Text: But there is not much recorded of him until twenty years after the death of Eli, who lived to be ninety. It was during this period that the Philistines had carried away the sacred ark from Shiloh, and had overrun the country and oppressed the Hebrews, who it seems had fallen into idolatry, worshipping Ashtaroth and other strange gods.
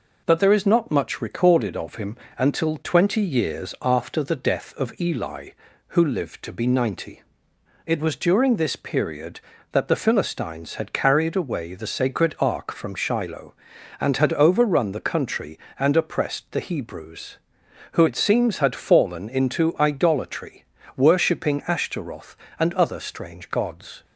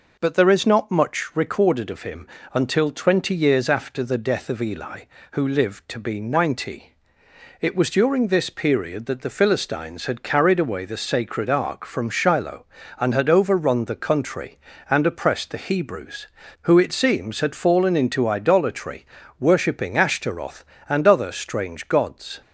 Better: neither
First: pauses between "him" and "until"; slight; at 2.1 s; 0.22 s long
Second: pauses between "him" and "until"; slight; at 2.2 s; 0.26 s long

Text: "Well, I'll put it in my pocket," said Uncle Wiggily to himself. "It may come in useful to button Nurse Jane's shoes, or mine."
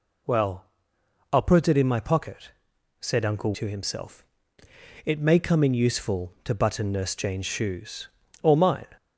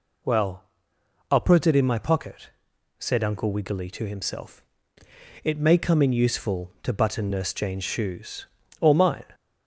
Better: second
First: skips "Wiggily"; at 3.5 s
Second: none

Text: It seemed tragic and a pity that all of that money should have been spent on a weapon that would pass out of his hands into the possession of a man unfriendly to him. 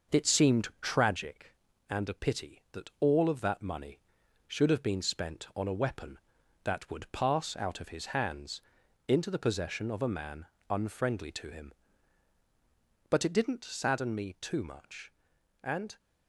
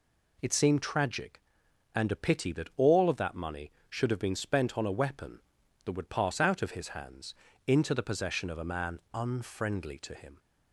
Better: second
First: starts louder than the rest; until 1.2 s; 6 dB // pauses between "hands" and "into"; at 8.6 s; 0.44 s long // pauses between "man" and "unfriendly"; slight; at 10.4 s; 0.24 s long // goes on to say "But it didn't sadden me too much and"; strong; from 13.1 s on; 2.8 s long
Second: pauses between "hands" and "into"; slight; at 7.3 s; 0.32 s long

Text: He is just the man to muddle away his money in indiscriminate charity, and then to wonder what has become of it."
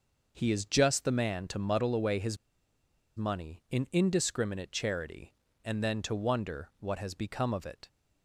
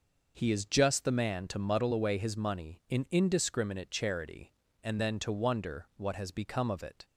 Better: second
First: pauses between "his" and "money"; noticeable; at 2.3 s; 0.81 s long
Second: none

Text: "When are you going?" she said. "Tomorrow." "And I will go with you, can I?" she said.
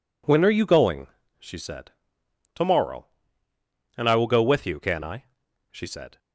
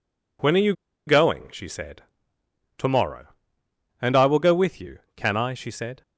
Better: first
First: none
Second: pauses between "you" and "going"; slight; at 0.7 s; 0.34 s long

